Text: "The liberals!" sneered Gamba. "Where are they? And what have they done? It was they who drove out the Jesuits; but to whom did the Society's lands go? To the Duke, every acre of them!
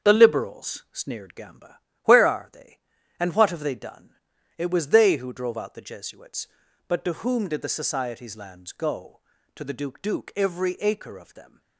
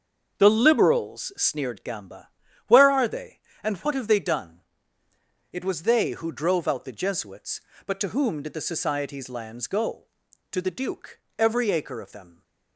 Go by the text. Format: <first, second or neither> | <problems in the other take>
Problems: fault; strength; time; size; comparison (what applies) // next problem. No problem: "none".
second | starts louder than the rest; strong; until 1.1 s; 7 dB; also in the second // says "Duke" twice; at 9.9 s